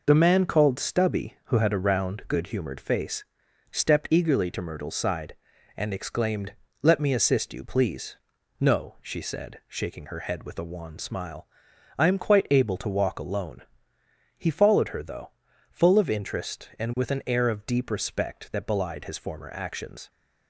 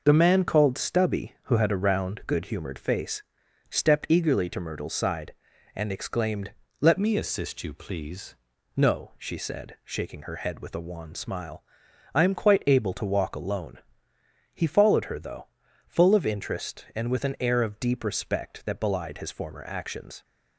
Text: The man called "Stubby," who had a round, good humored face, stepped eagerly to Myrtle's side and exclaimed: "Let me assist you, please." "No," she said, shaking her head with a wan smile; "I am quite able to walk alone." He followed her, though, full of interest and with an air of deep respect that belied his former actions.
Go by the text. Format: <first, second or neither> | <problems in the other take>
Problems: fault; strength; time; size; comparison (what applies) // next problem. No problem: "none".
first | changes voice from "me" to "please"; from 6.9 to 8.3 s; 1.4 s long